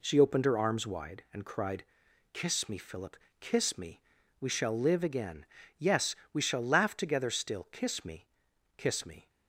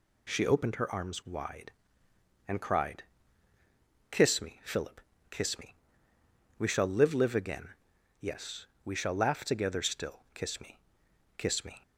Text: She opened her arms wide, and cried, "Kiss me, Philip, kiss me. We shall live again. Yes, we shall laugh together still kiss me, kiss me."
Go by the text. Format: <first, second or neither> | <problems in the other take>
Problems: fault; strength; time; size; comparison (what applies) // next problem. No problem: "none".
first | says "live" twice; at 7.1 s // pauses between "still" and "kiss"; slight; at 10.1 s; 0.16 s long